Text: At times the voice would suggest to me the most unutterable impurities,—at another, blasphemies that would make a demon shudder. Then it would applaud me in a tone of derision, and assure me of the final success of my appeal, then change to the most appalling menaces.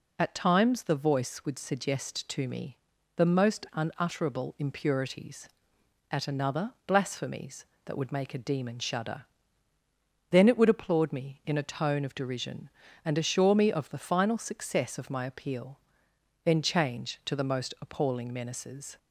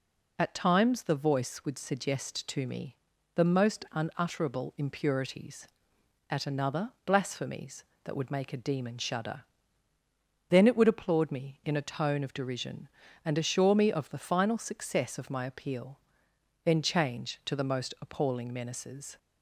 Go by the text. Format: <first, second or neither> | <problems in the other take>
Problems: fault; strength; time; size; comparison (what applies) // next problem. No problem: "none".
neither | pauses between "me" and "the"; the same in both